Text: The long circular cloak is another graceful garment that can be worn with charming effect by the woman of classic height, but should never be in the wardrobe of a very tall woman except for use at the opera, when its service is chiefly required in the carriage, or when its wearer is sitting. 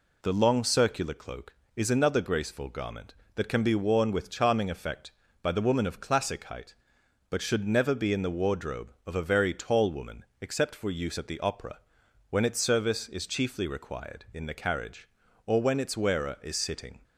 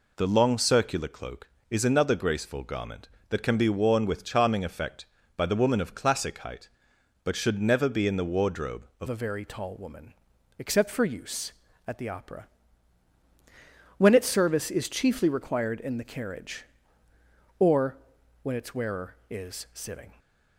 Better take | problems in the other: first | changes voice at "a"; from 9.0 s on; 11.1 s long // pauses between "woman" and "except"; noticeable; at 10.1 s; 0.48 s long; slight in the first // pauses between "or" and "when"; noticeable; at 17.9 s; 0.48 s long

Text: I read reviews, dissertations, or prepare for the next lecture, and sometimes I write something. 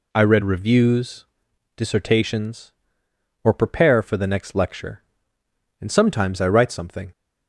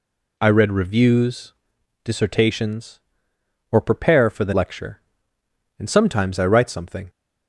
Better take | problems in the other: first | skips "next"; at 4.5 s

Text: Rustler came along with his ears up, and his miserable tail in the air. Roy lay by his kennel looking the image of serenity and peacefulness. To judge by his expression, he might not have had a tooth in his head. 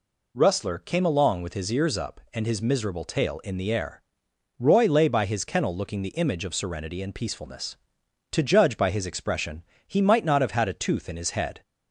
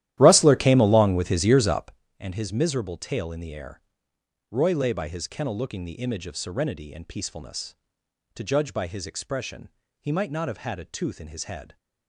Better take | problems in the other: first | starts louder than the rest; strong; until 2.0 s; 13.5 dB

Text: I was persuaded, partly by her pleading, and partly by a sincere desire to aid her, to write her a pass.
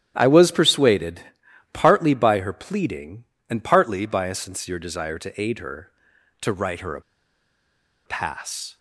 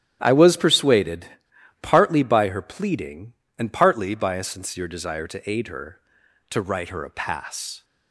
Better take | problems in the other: second | starts louder than the rest; strong; until 1.1 s; 11 dB; strong in the second // pauses between "a" and "pass"; at 7.0 s; 1.0 s long

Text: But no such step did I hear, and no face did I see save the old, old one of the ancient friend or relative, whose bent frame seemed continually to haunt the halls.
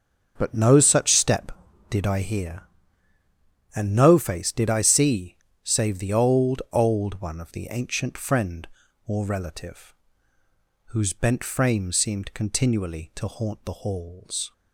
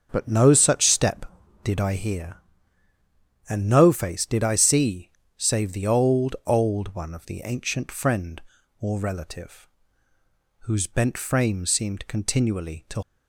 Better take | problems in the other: first | starts louder than the rest; until 1.1 s; 7 dB; also in the first // pauses between "see" and "save"; slight; at 5.0 s; 0.30 s long; slight in the first // stops before "haunt the halls"; at 13.0 s

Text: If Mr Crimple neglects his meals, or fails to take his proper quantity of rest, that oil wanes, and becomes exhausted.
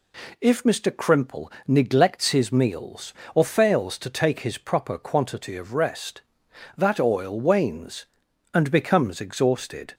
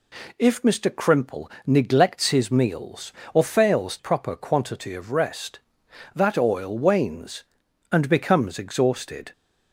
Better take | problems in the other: first | pauses between "Crimple" and "neglects"; slight; at 1.4 s; 0.16 s long; slight in the first // skips "to take his"; at 3.9 s

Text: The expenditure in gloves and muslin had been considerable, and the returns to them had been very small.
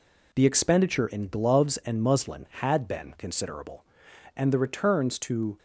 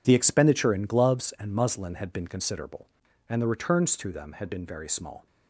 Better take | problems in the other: second | stops before "them had been very small"; at 5.5 s

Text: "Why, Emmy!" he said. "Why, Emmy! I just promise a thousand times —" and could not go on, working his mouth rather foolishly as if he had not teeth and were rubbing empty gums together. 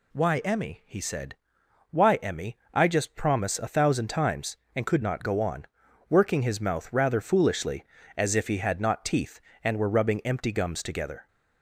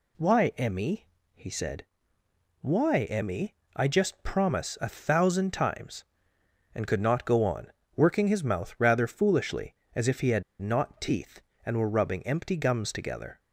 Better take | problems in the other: first | pauses between "had" and "not"; slight; at 10.4 s; 0.18 s long

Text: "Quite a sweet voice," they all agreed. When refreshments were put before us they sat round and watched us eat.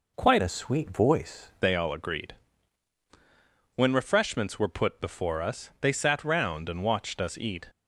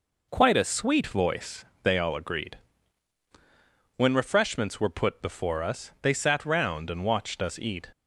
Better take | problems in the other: second | changes voice from "a" to "voice"; from 0.3 to 1.4 s; 1.1 s long

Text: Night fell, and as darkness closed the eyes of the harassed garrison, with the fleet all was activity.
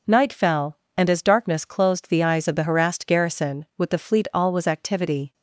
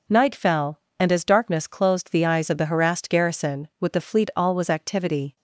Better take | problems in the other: neither | none

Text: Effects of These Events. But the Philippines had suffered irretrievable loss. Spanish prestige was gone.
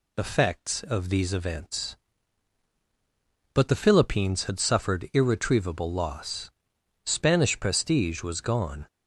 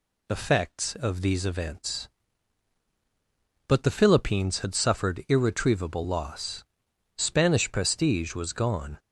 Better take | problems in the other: neither | none

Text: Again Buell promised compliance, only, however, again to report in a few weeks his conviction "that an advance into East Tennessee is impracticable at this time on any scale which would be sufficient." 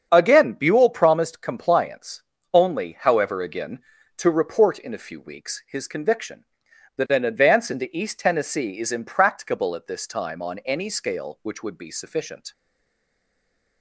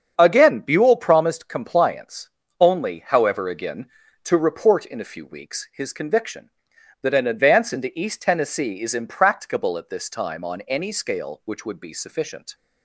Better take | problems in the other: second | starts louder than the rest; strong; until 1.1 s; 7.5 dB; strong in the second // stays silent after the last word; noticeable; from 12.5 s on; 1.3 s long

